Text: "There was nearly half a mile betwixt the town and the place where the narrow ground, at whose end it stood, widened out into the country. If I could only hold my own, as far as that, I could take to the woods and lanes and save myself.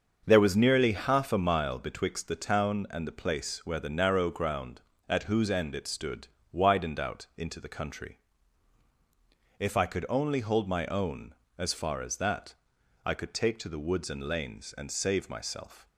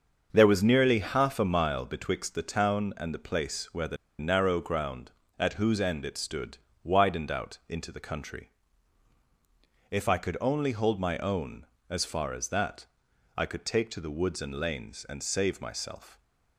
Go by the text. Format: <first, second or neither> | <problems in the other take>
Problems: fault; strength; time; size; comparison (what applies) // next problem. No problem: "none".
first | starts louder than the rest; until 1.3 s; 6.5 dB; also in the first // pauses between "the" and "narrow"; slight; at 3.9 s; 0.22 s long